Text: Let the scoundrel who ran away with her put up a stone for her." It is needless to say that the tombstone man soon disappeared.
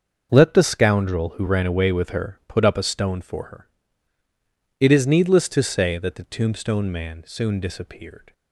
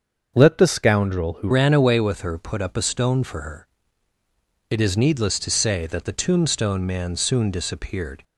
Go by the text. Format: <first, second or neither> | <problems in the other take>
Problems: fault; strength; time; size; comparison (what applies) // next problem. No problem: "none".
first | starts louder than the rest; until 1.4 s; 6.5 dB; also in the first // changes voice at "ran"; from 1.5 s on; 6.7 s long